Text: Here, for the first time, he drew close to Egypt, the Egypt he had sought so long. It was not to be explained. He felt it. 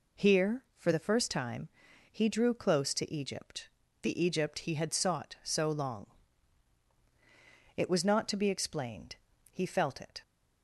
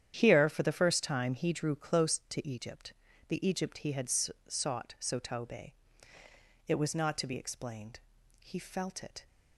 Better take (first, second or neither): first